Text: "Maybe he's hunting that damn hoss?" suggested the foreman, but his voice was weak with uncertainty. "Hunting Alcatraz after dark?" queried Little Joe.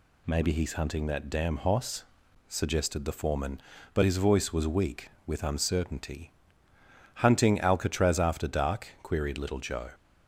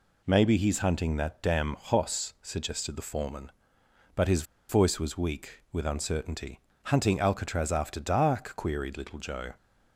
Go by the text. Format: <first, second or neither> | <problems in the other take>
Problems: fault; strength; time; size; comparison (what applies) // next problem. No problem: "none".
first | pauses between "his" and "voice"; slight; at 4.4 s; 0.26 s long